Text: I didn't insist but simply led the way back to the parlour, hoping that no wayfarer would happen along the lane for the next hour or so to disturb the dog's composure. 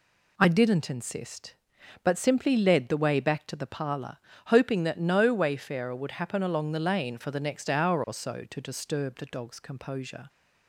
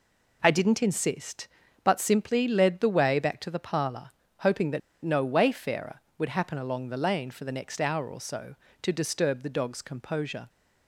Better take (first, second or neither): first